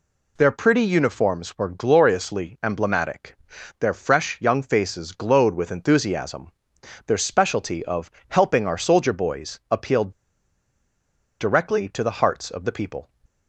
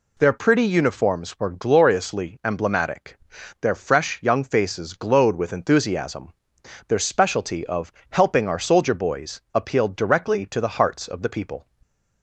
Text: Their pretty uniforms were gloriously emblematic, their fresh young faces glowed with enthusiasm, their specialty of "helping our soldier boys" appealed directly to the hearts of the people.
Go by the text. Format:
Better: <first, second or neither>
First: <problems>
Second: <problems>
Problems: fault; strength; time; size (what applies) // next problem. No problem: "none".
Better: second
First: pauses between "of" and "helping"; slight; at 8.1 s; 0.16 s long // pauses between "appealed" and "directly"; strong; at 10.1 s; 1.2 s long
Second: pauses between "of" and "helping"; slight; at 7.9 s; 0.16 s long